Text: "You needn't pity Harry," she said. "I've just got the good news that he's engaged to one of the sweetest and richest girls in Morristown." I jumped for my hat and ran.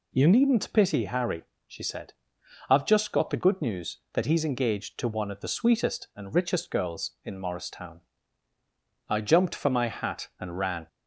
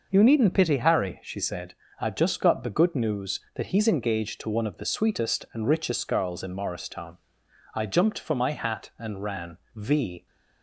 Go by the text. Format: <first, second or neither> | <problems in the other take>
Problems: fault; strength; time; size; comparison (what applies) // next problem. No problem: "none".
first | goes on to say "V"; from 9.7 s on; 0.50 s long